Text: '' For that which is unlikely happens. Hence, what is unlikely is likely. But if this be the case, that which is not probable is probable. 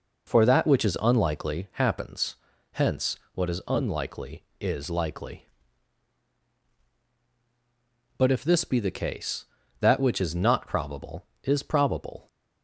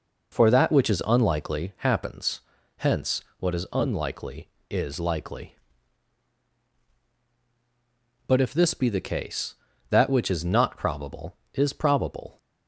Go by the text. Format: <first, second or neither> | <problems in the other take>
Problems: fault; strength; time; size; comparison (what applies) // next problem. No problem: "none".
neither | none